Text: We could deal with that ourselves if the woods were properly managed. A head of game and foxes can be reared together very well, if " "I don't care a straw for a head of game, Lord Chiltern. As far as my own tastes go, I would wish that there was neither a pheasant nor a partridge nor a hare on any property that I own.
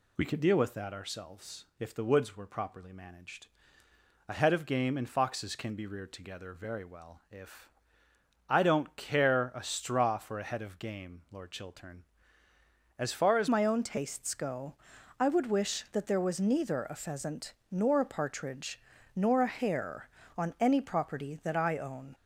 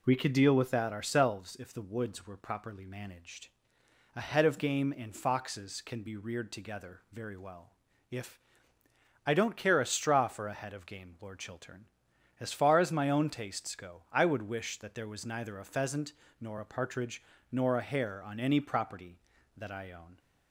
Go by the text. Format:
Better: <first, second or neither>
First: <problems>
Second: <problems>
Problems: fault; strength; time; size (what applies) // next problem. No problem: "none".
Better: second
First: changes voice at "my"; from 13.4 s on; 8.7 s long // pauses between "pheasant" and "nor"; slight; at 17.5 s; 0.18 s long // pauses between "partridge" and "nor"; slight; at 18.8 s; 0.36 s long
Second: pauses between "pheasant" and "nor"; slight; at 16.1 s; 0.26 s long // pauses between "partridge" and "nor"; slight; at 17.2 s; 0.30 s long